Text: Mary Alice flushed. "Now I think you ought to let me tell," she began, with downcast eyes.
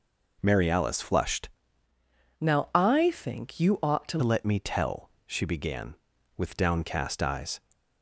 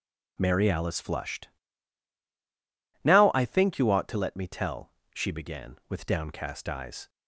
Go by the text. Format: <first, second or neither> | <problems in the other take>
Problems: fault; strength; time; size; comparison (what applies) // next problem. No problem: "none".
second | changes voice from "Now" to "to"; from 2.3 to 4.1 s; 1.8 s long